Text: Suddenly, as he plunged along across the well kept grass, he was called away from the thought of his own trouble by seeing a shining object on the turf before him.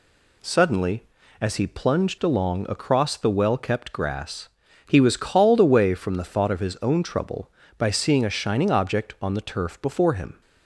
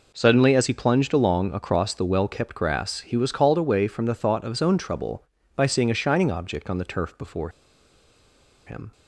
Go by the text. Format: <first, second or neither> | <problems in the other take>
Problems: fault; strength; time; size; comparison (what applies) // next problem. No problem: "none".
first | pauses between "before" and "him"; at 7.4 s; 1.1 s long